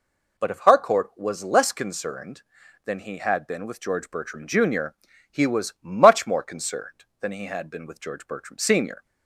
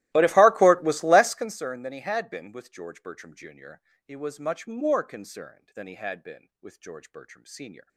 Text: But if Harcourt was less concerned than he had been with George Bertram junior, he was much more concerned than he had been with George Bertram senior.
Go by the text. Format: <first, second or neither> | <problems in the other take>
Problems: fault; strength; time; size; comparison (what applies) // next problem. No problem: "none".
first | starts louder than the rest; strong; until 1.6 s; 16.5 dB